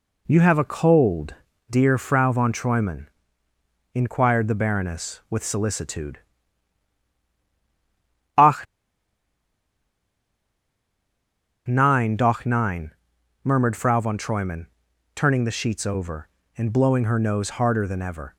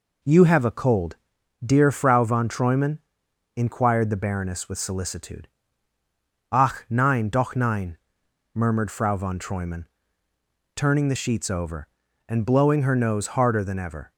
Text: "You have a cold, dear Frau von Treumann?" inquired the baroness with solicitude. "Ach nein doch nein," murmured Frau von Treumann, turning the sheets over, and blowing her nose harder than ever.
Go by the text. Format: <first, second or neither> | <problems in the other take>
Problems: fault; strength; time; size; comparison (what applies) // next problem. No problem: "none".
second | pauses between "Ach" and "nein"; strong; at 8.6 s; 3.0 s long